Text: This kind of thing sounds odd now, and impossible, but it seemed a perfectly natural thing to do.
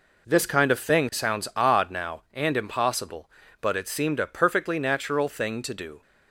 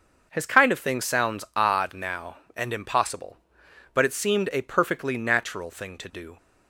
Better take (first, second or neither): first